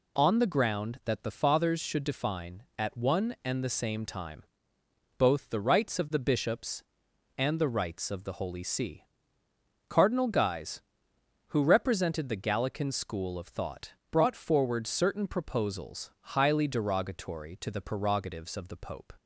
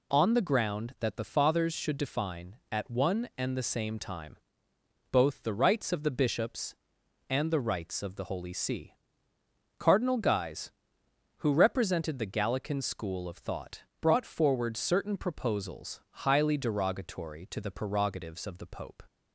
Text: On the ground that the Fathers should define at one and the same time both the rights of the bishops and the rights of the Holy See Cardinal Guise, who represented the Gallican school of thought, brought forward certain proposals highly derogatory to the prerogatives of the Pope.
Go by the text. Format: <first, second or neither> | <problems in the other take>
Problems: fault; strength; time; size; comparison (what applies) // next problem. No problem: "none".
neither | pauses between "time" and "both"; noticeable; the same in both // pauses between "See" and "Cardinal"; noticeable; the same in both